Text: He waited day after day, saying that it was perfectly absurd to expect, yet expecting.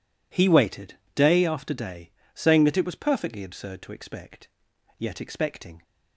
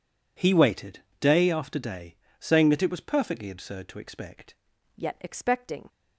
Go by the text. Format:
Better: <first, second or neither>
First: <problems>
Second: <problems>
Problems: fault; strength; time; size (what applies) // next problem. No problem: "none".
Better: first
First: pauses between "waited" and "day"; slight; at 0.9 s; 0.20 s long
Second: pauses between "waited" and "day"; slight; at 0.9 s; 0.20 s long // changes voice at "yet"; from 4.9 s on; 0.9 s long